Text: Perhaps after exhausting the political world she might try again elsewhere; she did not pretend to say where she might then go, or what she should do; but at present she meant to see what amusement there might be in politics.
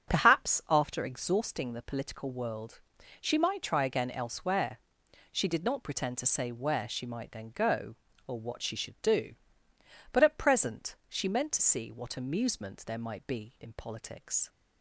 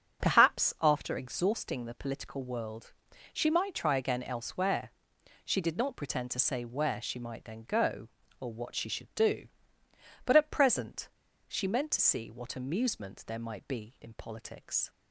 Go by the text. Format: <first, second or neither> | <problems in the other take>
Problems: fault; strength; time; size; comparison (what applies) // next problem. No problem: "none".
first | starts louder than the rest; until 1.3 s; 7 dB; also in the first // pauses between "world" and "she"; at 2.9 s; 0.42 s long; also in the first // pauses between "present" and "she"; at 11.0 s; 0.40 s long